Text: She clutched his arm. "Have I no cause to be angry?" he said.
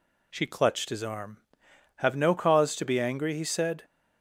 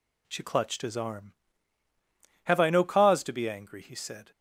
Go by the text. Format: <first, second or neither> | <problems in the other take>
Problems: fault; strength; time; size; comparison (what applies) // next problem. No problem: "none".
second | skips "I"; at 2.1 s